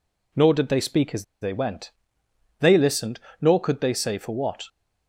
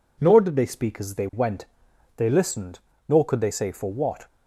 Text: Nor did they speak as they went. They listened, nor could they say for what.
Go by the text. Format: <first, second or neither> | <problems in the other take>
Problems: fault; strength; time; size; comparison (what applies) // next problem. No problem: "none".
second | pauses between "as" and "they"; slight; at 1.2 s; 0.17 s long